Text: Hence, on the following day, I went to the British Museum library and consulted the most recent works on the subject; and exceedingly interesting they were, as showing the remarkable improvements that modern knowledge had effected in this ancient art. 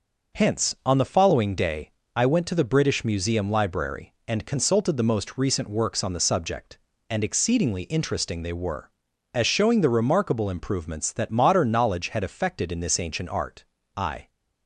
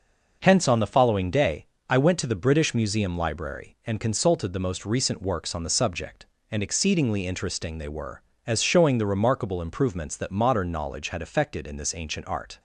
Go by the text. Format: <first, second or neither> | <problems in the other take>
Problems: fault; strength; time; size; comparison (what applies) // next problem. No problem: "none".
second | goes on to say "I"; slight; from 13.9 s on; 0.34 s long